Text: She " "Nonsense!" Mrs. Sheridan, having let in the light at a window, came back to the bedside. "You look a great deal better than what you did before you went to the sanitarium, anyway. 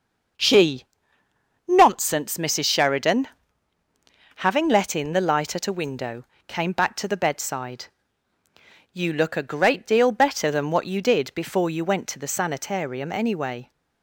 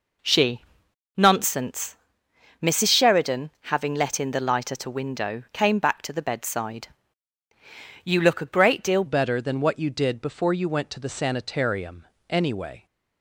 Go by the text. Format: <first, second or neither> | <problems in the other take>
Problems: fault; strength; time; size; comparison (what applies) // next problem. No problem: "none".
first | changes voice at "better"; from 9.0 s on; 3.8 s long